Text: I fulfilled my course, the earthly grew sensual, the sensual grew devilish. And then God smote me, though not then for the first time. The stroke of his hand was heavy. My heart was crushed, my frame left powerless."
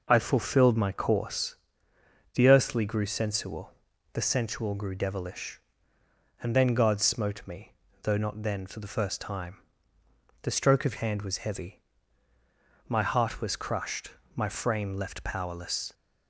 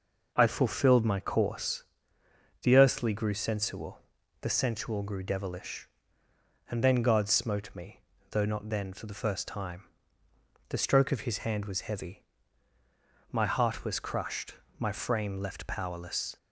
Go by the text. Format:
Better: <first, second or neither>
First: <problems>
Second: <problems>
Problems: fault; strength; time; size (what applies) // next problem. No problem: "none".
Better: second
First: skips "his"; at 10.9 s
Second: none